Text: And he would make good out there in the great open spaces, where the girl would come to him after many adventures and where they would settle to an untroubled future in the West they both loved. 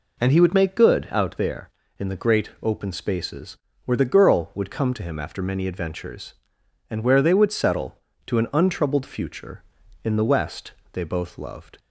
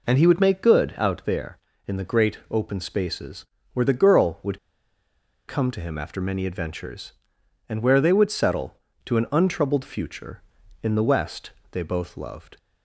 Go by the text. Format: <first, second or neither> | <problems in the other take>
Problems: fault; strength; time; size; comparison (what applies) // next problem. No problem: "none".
first | pauses between "would" and "come"; noticeable; at 4.5 s; 0.90 s long // pauses between "West" and "they"; slight; at 11.5 s; 0.20 s long; slight in the first